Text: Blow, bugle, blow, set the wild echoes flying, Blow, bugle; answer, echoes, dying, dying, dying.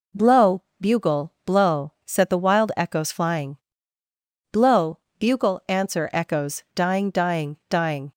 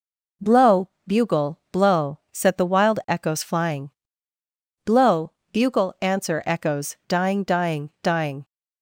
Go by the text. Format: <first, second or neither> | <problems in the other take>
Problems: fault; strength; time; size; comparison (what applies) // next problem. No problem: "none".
neither | none